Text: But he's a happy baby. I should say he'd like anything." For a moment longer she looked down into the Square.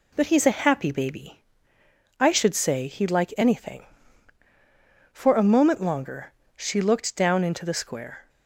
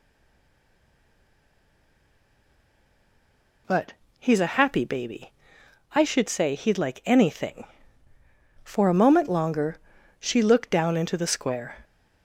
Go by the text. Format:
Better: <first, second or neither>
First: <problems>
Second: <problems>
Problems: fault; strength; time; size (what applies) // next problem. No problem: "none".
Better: first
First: pauses between "longer" and "she"; slight; at 6.3 s; 0.22 s long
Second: stays silent before the first word; strong; until 3.6 s; 3.6 s long // pauses between "But" and "he's"; slight; at 3.9 s; 0.26 s long // pauses between "longer" and "she"; at 9.7 s; 0.42 s long